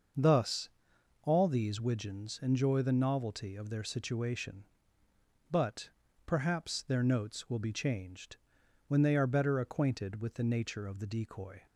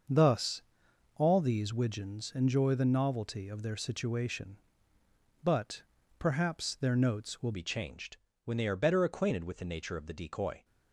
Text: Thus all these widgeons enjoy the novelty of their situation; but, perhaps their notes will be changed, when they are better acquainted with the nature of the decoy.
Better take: first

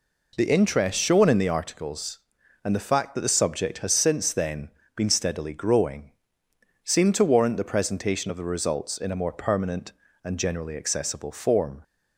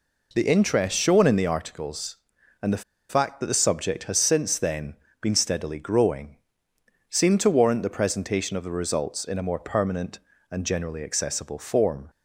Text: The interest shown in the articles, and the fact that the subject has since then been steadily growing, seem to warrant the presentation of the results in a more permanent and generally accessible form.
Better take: first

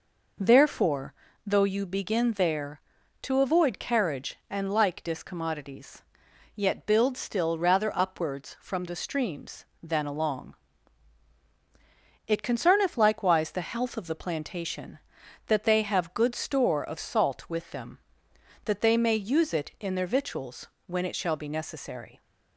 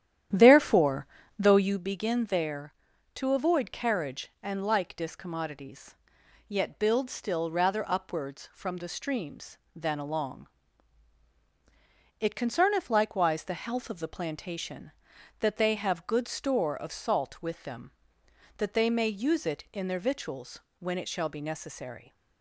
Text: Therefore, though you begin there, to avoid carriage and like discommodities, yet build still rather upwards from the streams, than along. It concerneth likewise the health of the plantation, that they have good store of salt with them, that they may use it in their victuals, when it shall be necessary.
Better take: first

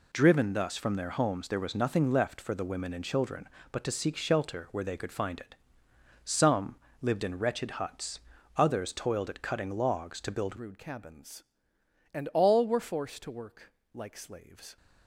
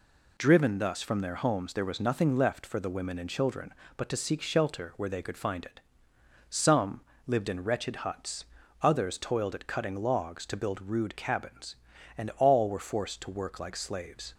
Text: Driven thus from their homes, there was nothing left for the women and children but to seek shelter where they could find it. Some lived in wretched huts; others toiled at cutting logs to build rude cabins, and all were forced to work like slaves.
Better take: second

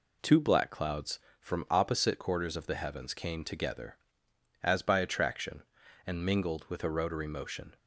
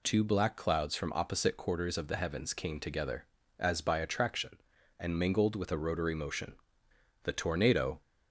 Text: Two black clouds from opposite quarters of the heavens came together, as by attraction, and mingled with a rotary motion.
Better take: first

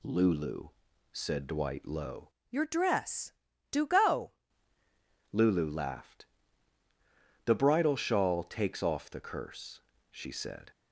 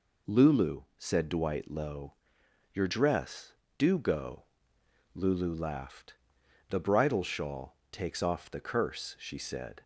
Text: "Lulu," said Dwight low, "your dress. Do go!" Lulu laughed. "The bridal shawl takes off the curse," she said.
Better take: second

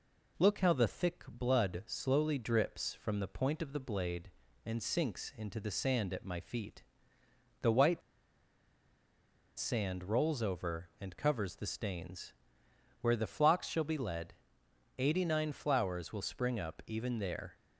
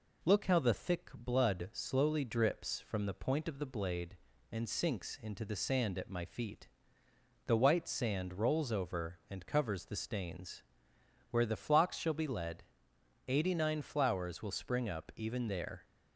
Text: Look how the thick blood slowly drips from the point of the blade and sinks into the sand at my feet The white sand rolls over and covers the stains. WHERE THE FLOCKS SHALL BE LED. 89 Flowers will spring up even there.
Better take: second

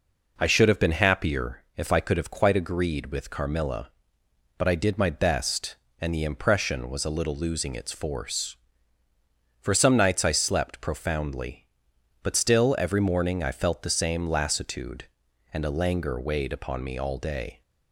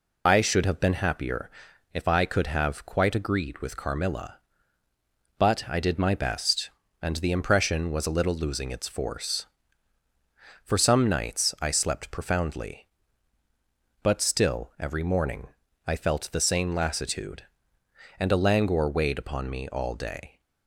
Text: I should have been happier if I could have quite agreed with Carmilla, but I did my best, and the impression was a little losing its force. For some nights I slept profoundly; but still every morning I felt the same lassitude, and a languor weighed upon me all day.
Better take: first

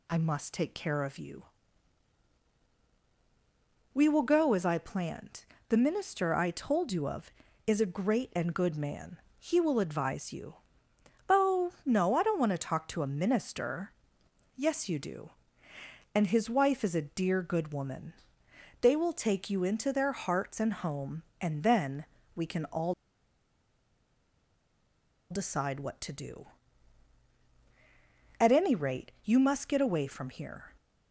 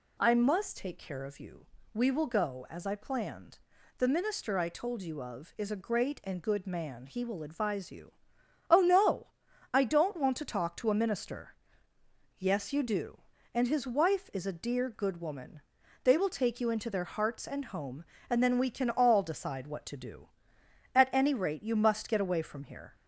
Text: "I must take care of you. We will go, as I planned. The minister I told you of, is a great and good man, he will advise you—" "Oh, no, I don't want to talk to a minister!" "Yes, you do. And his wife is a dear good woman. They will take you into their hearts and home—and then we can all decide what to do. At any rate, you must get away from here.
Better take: second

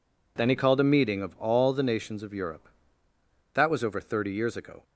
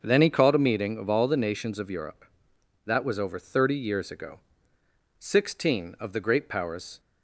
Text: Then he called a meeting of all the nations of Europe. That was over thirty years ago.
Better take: first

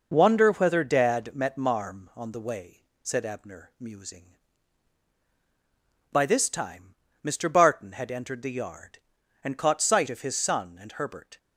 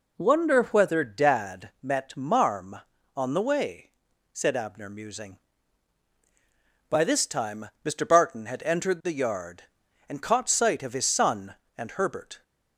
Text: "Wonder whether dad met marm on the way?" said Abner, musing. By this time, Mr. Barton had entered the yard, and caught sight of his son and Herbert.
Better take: neither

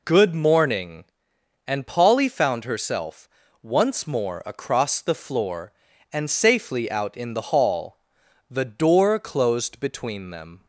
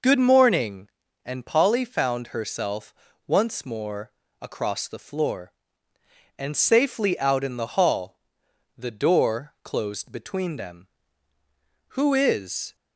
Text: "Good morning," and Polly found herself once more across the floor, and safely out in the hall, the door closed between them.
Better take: first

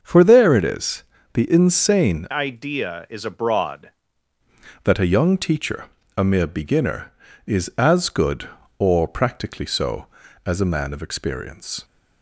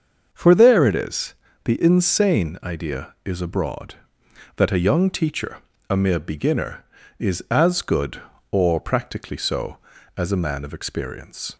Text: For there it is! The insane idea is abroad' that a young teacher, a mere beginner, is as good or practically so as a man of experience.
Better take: second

